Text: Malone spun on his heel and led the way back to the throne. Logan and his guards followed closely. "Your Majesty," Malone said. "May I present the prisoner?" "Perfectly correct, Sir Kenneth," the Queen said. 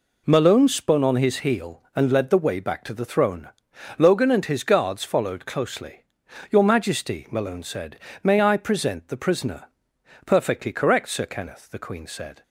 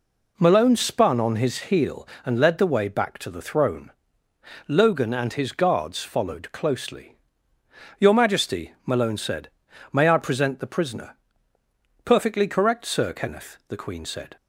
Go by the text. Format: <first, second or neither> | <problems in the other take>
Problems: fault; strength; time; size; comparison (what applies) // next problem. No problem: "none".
neither | none